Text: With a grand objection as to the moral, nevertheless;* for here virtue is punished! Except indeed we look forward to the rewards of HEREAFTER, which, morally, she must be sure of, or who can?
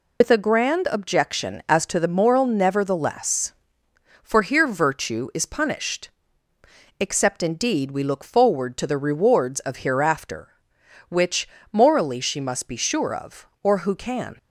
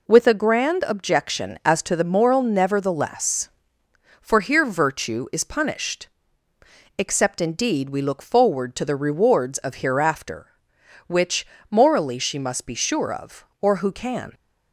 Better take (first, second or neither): second